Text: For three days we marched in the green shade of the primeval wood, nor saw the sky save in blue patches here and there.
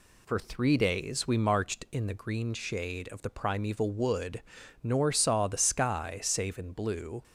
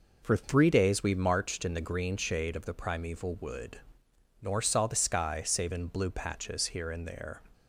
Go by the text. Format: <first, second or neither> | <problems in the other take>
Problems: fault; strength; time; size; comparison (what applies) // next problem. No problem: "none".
second | stops before "patches here and there"; at 7.2 s